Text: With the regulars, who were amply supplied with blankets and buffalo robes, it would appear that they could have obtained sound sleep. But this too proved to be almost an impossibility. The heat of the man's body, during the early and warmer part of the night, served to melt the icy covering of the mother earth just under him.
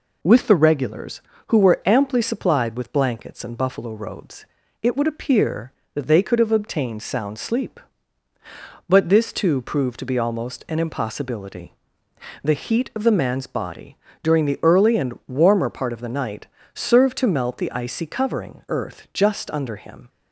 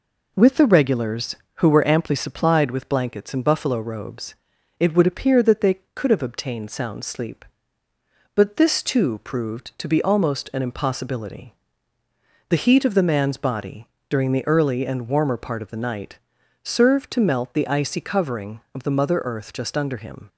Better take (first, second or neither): second